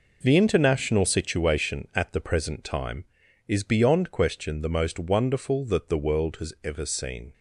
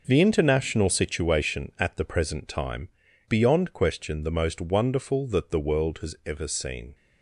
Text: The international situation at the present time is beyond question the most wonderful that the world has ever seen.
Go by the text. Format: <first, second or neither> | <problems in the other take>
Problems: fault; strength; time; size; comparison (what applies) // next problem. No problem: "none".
first | skips "is"; at 3.0 s